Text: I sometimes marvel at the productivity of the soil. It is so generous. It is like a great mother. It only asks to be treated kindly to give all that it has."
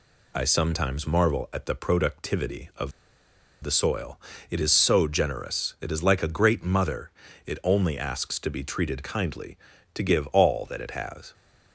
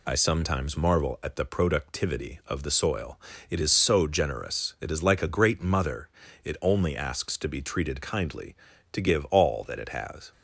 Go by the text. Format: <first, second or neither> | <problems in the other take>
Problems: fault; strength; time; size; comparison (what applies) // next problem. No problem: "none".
second | pauses between "of" and "the"; noticeable; at 2.9 s; 0.71 s long